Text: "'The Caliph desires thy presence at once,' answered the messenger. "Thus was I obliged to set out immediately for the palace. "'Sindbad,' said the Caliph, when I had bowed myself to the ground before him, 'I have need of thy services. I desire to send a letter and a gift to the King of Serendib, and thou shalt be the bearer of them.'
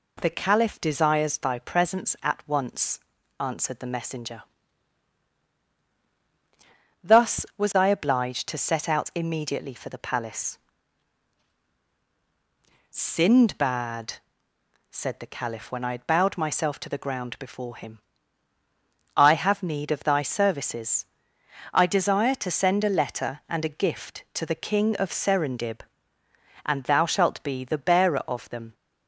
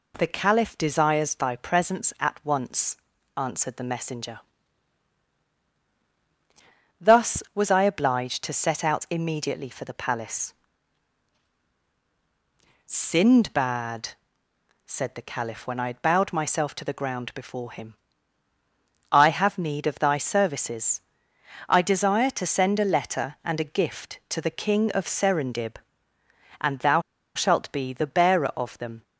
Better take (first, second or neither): first